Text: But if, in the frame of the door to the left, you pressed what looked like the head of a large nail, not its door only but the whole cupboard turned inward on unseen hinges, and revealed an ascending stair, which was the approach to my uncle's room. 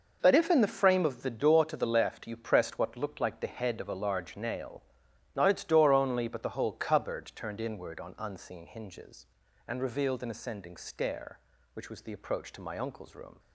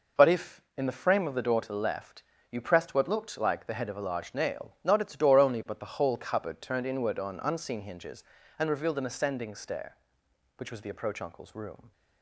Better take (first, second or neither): first